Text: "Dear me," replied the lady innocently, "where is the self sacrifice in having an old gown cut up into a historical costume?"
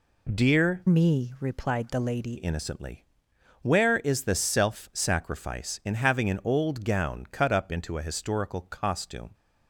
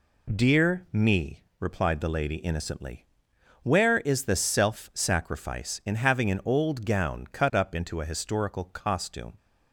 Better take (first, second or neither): second